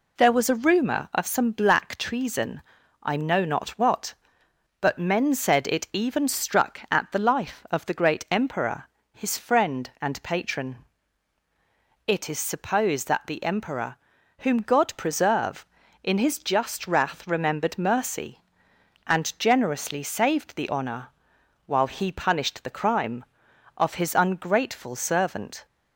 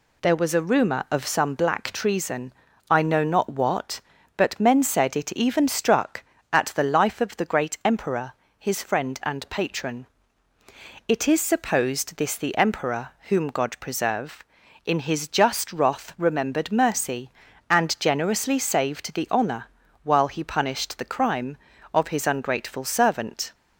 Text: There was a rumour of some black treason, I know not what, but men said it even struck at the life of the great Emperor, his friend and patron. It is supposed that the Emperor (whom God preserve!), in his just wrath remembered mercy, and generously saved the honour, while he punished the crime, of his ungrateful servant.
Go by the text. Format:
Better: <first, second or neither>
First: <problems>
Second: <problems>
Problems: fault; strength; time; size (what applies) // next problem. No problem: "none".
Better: first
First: none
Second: says "this" for "that"; at 12.1 s